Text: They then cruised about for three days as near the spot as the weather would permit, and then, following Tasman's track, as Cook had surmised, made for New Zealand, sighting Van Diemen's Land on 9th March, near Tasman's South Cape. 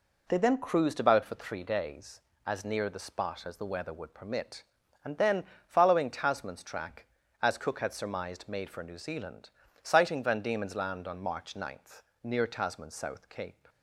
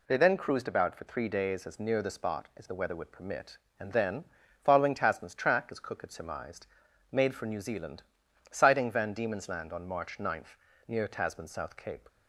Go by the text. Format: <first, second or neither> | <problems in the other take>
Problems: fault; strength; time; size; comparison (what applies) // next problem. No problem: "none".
neither | none